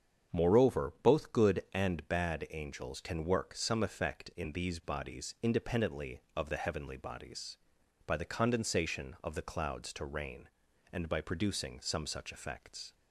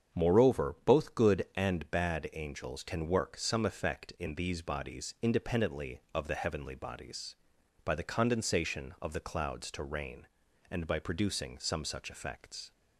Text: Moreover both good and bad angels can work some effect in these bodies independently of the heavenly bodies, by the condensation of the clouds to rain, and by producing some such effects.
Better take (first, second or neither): neither